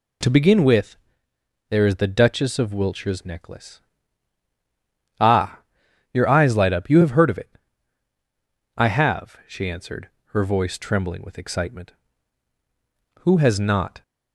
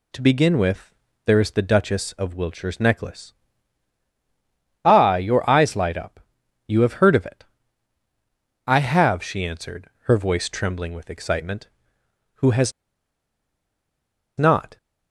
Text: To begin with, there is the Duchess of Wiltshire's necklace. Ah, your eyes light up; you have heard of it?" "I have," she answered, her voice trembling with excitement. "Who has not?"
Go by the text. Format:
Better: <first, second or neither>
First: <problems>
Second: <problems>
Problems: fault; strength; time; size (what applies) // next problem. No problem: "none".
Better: first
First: none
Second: pauses between "has" and "not"; strong; at 12.7 s; 1.6 s long